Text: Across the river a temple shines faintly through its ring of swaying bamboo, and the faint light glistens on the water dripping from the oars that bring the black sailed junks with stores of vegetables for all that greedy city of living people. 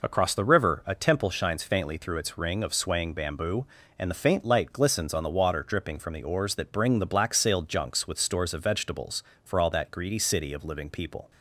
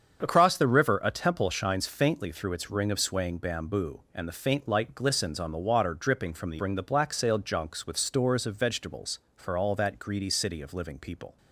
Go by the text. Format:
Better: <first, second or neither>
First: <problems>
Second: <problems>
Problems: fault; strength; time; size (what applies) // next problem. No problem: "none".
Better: first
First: none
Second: starts louder than the rest; strong; until 1.2 s; 7 dB // skips "oars that"; at 6.5 s